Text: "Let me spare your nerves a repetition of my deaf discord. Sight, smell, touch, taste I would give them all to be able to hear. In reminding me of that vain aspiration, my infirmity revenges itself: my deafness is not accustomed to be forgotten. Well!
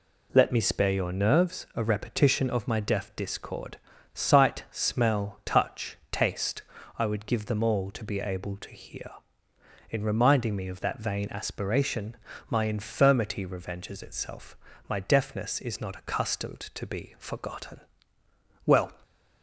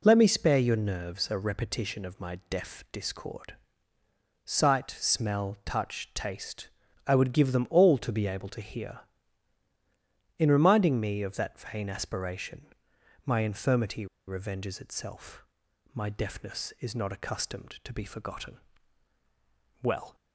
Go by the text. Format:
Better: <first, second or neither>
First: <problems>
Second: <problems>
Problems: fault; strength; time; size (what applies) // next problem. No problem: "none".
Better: first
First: pauses between "taste" and "I"; slight; at 6.6 s; 0.34 s long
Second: pauses between "taste" and "I"; at 6.6 s; 0.40 s long // pauses between "infirmity" and "revenges"; slight; at 14.0 s; 0.22 s long